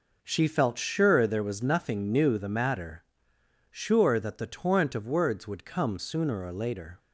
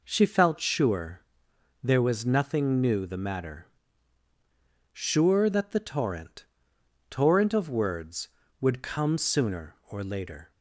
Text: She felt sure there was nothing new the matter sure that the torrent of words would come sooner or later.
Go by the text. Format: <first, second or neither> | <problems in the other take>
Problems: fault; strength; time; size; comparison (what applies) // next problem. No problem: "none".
first | pauses between "sure" and "there"; noticeable; at 1.2 s; 0.60 s long // pauses between "matter" and "sure"; at 3.6 s; 1.2 s long; noticeable in the first // says "torrent" twice; at 7.0 s